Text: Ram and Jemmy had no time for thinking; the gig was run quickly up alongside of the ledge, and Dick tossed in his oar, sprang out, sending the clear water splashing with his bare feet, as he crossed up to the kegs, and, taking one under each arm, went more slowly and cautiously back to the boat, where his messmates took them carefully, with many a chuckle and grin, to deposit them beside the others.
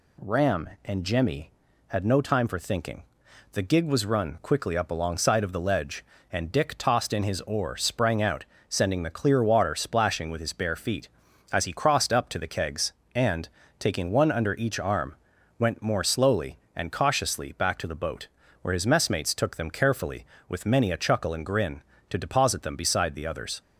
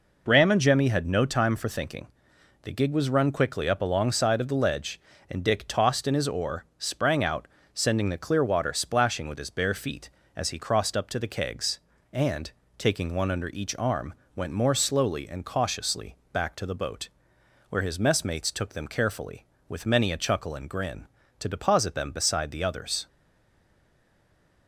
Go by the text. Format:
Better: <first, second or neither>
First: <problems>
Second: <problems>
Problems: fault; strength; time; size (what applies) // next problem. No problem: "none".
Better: first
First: none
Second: pauses between "cautiously" and "back"; slight; at 16.1 s; 0.16 s long // stays silent after the last word; noticeable; from 23.0 s on; 1.6 s long